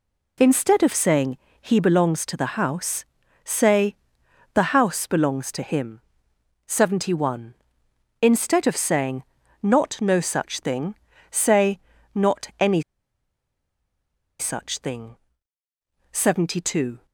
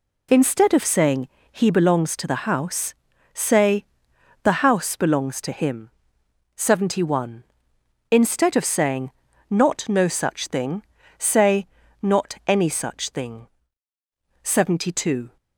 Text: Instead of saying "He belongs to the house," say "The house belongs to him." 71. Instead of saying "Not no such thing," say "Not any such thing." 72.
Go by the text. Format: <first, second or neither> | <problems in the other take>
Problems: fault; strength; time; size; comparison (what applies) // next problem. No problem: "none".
second | pauses between "saying" and "He"; slight; at 1.3 s; 0.24 s long; slight in the second // pauses between "say" and "The"; noticeable; at 3.9 s; 0.56 s long; noticeable in the second // pauses between "saying" and "Not"; at 9.2 s; 0.38 s long; also in the second // pauses between "say" and "Not"; slight; at 11.8 s; 0.34 s long; slight in the second // pauses between "any" and "such"; strong; at 12.8 s; 1.5 s long